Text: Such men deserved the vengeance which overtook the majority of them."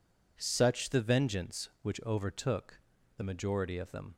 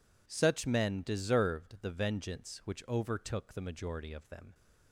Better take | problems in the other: second | skips "men deserved"; at 0.9 s // pauses between "overtook" and "the"; at 2.7 s; 0.38 s long

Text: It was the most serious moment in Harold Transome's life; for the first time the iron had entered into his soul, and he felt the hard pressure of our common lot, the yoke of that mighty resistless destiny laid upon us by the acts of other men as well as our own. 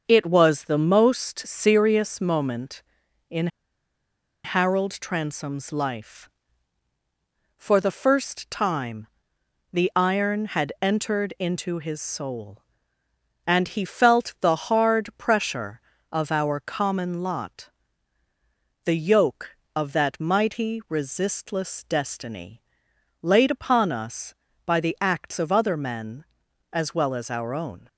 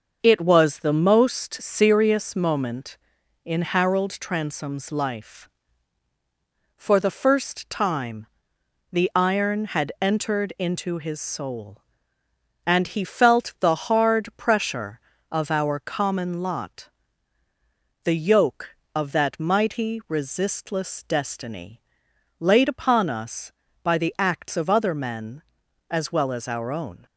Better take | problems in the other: second | starts louder than the rest; until 1.0 s; 6.5 dB; also in the second // pauses between "in" and "Harold"; noticeable; at 3.4 s; 0.97 s long // pauses between "time" and "the"; noticeable; at 9.0 s; 0.64 s long; noticeable in the second // pauses between "destiny" and "laid"; noticeable; at 22.6 s; 0.60 s long; noticeable in the second

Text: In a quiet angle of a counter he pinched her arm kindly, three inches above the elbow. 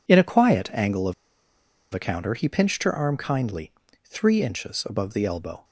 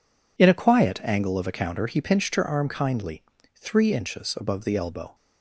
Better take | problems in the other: second | pauses between "of" and "a"; noticeable; at 1.1 s; 0.80 s long

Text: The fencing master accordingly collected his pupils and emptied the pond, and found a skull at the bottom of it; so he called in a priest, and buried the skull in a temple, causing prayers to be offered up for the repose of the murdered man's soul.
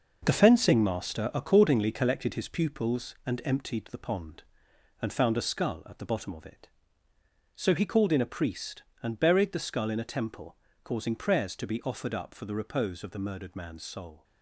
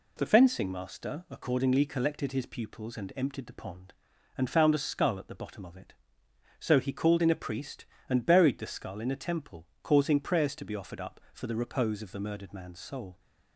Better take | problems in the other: second | gets quieter; strong; throughout; 8 dB

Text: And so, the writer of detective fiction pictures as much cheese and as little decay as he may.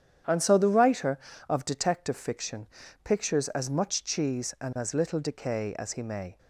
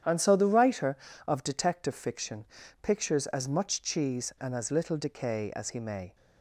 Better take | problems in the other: neither | starts louder than the rest; strong; the same in both // pauses between "fiction" and "pictures"; slight; the same in both

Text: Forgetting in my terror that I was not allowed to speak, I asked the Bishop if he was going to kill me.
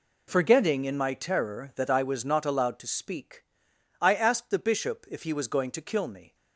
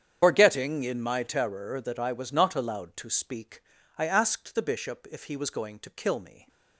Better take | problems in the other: first | loses the start of "Forgetting"; at 0.2 s; 145 ms // starts louder than the rest; strong; until 1.2 s; 8.5 dB

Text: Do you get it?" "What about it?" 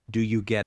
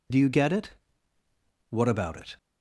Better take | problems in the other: second | stops before "it What about it"; at 0.6 s

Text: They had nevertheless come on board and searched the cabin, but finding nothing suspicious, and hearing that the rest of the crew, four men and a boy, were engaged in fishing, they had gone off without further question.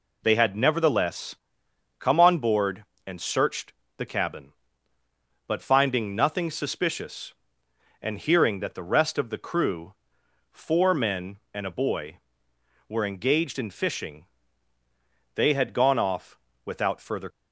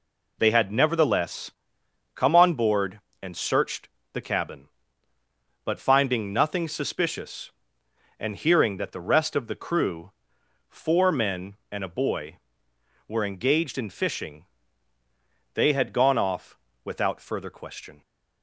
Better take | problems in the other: second | pauses between "nevertheless" and "come"; noticeable; at 1.3 s; 0.64 s long; noticeable in the second // pauses between "searched" and "the"; slight; at 3.7 s; 0.24 s long; slight in the second // pauses between "off" and "without"; slight; at 16.3 s; 0.26 s long; slight in the second // stops before "question"; at 17.3 s

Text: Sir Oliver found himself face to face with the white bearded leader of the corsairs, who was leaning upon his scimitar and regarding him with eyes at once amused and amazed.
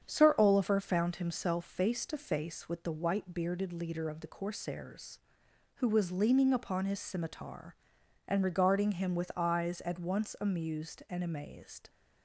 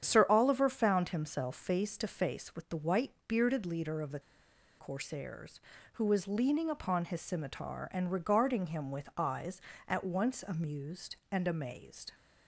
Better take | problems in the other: first | starts louder than the rest; strong; until 1.0 s; 8.5 dB; strong in the first // pauses between "the" and "corsairs"; noticeable; at 4.1 s; 0.59 s long

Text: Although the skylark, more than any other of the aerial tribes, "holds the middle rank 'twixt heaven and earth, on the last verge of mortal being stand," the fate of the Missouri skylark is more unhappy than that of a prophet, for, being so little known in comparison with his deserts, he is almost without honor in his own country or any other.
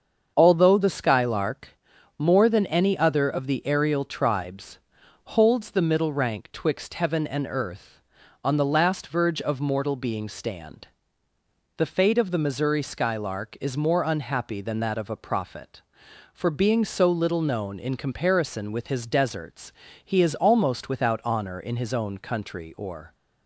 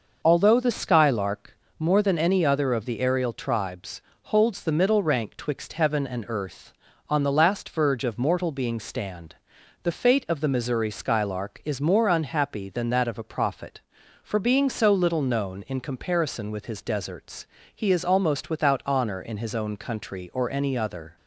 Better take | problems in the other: second | starts louder than the rest; until 1.3 s; 7 dB // stops before "any other"; at 23.1 s

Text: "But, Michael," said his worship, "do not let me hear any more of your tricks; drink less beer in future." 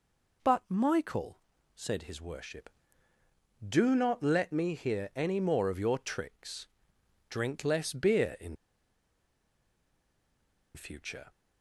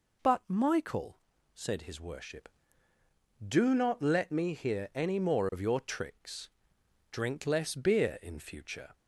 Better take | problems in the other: second | pauses between "in" and "future"; strong; at 8.5 s; 2.1 s long

